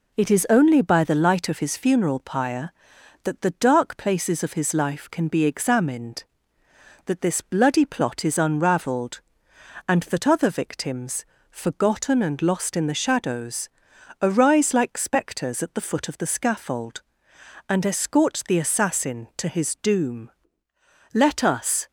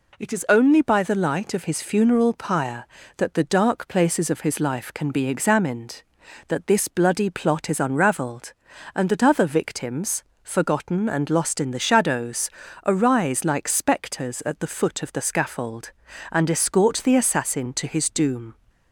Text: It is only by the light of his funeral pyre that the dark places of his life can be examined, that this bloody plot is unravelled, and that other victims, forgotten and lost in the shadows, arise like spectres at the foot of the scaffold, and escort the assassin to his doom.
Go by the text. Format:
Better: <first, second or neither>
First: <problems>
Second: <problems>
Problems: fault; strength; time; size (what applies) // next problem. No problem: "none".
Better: second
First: goes on to say "Let us"; noticeable; from 21.1 s on; 0.76 s long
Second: none